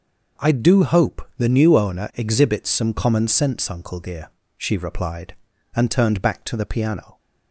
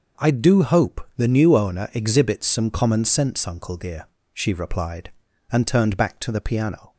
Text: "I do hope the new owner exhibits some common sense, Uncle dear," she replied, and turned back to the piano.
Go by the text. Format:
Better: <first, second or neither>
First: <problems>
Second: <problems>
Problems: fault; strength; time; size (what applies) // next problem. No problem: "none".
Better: neither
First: none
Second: none